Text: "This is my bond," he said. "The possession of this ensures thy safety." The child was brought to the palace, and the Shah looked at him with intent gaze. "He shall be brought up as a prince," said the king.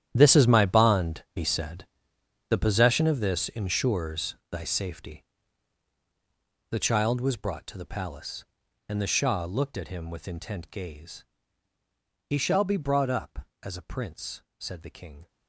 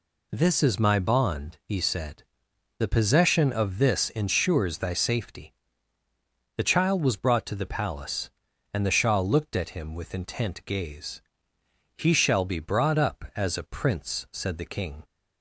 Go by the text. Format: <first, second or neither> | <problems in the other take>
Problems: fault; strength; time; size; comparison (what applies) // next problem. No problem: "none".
second | gets quieter; strong; throughout; 16 dB